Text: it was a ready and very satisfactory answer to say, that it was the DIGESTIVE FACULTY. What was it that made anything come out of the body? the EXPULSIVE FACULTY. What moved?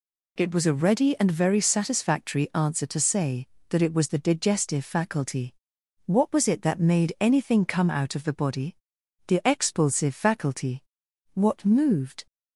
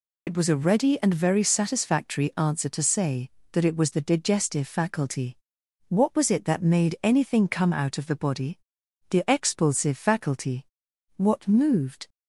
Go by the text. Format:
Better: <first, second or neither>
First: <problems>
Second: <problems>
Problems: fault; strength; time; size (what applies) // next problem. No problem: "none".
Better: first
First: none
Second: loses the start of "it"; at 0.2 s; 65 ms